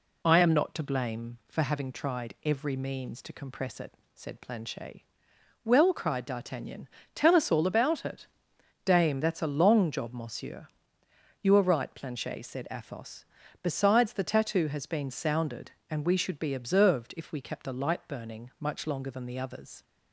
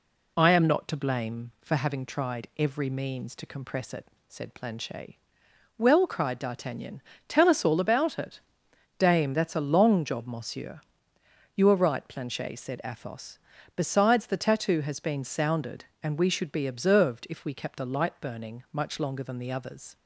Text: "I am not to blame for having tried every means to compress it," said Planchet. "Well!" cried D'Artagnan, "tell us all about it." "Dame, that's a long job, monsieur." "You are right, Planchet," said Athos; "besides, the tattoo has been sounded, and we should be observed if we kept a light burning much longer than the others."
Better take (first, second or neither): neither